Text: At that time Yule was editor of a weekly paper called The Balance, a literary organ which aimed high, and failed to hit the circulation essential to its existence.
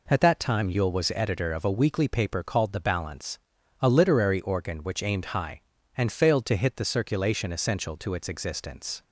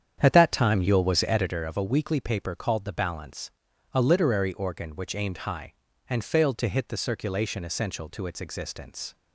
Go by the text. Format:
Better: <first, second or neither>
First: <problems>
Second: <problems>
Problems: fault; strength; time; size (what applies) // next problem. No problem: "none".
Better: first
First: none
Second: starts louder than the rest; strong; until 1.6 s; 8.5 dB